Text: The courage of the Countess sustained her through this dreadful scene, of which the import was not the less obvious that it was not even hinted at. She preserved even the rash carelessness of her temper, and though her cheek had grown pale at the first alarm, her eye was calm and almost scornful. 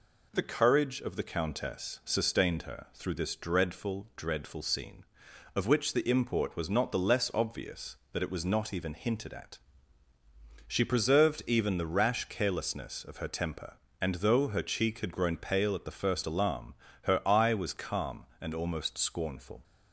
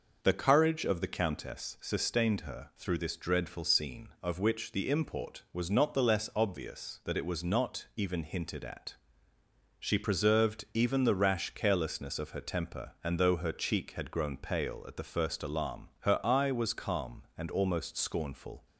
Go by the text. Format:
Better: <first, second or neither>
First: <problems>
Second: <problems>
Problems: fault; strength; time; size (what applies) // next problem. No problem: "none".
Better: second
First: says "dreadful" twice; at 4.1 s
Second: none